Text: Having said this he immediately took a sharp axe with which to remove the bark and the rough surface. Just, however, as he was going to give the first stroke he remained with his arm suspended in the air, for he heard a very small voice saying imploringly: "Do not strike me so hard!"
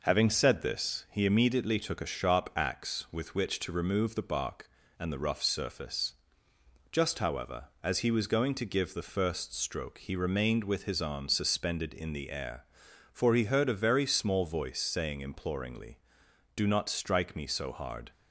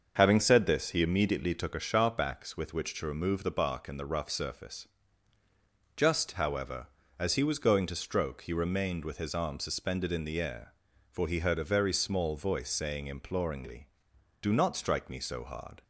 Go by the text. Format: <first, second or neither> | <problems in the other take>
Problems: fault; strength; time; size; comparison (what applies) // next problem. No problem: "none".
first | starts louder than the rest; until 1.1 s; 6.5 dB // skips "give the first"; at 7.9 s